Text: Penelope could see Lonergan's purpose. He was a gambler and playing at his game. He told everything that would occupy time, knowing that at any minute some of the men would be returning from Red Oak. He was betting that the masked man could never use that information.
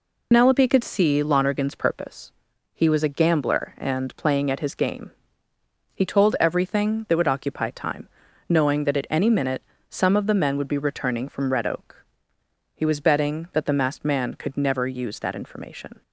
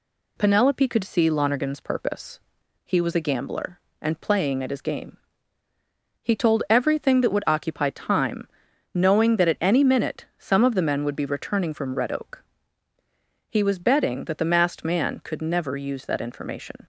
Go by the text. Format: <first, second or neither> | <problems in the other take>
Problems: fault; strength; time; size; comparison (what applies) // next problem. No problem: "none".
second | loses the start of "Penelope"; at 0.3 s; 75 ms // pauses between "minute" and "some"; slight; at 9.6 s; 0.26 s long